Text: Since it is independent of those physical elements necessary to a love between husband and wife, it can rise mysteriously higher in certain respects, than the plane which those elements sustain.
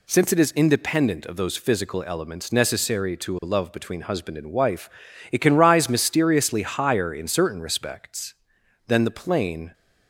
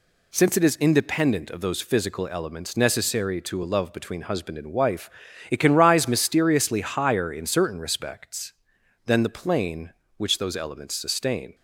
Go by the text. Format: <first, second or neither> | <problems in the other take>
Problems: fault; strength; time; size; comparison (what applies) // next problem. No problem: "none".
second | stops before "which those elements sustain"; at 9.7 s